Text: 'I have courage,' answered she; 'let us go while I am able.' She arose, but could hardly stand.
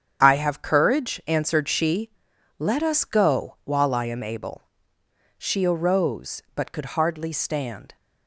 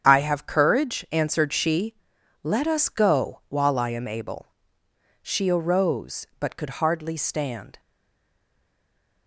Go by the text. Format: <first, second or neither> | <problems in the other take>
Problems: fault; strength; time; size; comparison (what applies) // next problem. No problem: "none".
first | starts louder than the rest; strong; until 1.1 s; 8 dB; strong in the first // stays silent after the last word; noticeable; from 7.7 s on; 1.5 s long